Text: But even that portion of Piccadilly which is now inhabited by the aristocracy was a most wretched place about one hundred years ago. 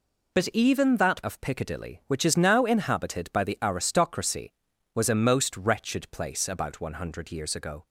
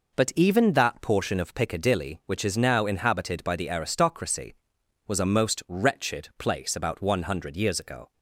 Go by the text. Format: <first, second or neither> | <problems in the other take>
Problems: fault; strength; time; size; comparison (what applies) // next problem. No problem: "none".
second | skips "portion"; at 1.2 s